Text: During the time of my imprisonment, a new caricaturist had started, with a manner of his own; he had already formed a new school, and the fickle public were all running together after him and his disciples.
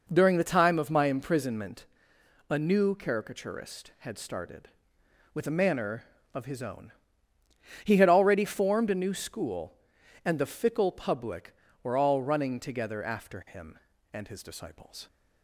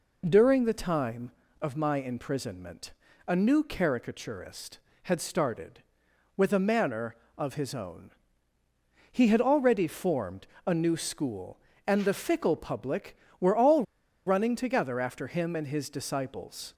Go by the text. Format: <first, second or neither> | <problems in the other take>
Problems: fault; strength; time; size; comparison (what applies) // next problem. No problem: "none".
first | pauses between "formed" and "a"; slight; at 10.4 s; 0.18 s long // pauses between "all" and "running"; at 13.8 s; 0.43 s long